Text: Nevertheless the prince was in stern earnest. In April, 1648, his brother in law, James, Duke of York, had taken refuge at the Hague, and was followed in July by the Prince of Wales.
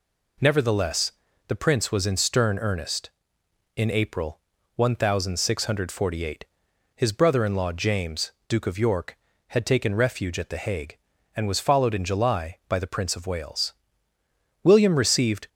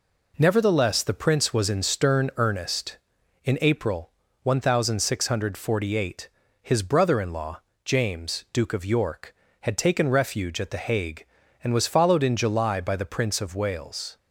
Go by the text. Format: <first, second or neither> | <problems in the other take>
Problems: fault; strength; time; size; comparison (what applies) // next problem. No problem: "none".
second | pauses between "Nevertheless" and "the"; slight; at 1.1 s; 0.36 s long // goes on to say "William received"; noticeable; from 14.6 s on; 0.86 s long